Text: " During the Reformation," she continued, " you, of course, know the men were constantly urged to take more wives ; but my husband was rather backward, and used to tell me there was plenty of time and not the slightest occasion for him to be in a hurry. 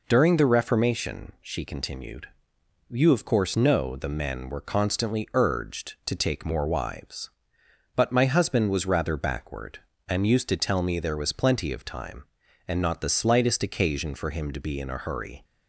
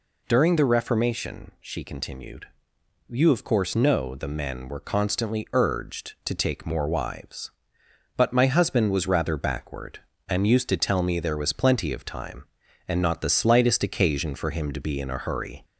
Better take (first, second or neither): first